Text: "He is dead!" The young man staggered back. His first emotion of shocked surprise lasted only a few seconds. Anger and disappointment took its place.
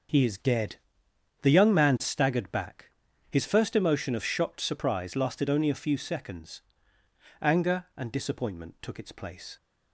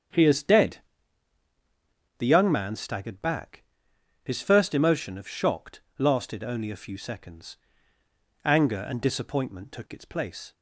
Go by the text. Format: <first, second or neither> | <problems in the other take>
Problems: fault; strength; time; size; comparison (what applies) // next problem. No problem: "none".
first | starts louder than the rest; strong; until 2.5 s; 8 dB // skips "surprise"; at 5.8 s